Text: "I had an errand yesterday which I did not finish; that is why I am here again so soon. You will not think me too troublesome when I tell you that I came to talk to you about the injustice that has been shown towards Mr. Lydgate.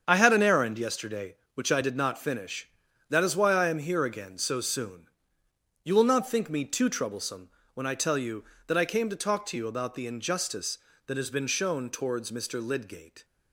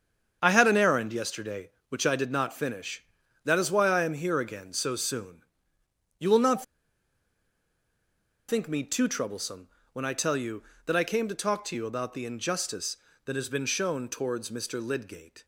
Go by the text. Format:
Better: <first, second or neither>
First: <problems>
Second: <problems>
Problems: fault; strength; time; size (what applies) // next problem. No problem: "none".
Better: first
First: starts louder than the rest; strong; until 1.0 s; 7.5 dB // pauses between "troublesome" and "when"; slight; at 7.4 s; 0.26 s long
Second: starts louder than the rest; strong; until 1.4 s; 7.5 dB // pauses between "not" and "think"; strong; at 6.6 s; 1.8 s long // pauses between "troublesome" and "when"; slight; at 9.6 s; 0.26 s long